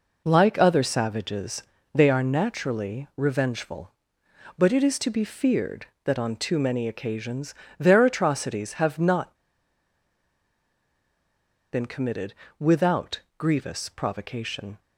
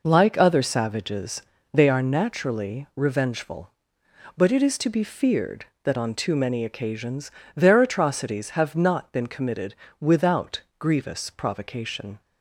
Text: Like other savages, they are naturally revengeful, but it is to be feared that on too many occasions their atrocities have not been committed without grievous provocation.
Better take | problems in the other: second | pauses between "occasions" and "their"; slight; at 7.5 s; 0.24 s long; slight in the second // pauses between "not" and "been"; strong; at 9.3 s; 2.3 s long // pauses between "committed" and "without"; slight; at 12.3 s; 0.26 s long; slight in the second // pauses between "without" and "grievous"; slight; at 13.1 s; 0.18 s long; slight in the second

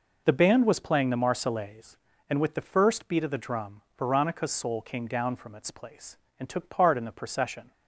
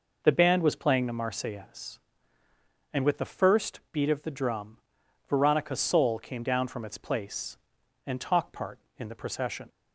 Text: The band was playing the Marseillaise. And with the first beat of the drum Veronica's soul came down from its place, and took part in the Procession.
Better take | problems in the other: first | pauses between "drum" and "Veronica's"; noticeable; at 4.7 s; 0.50 s long; slight in the first // says "talk" for "took"; at 8.2 s

